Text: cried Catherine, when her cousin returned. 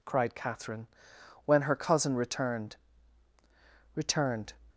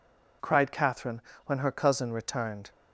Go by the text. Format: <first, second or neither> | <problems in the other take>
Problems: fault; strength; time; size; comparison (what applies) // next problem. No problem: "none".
second | says "returned" twice; at 3.9 s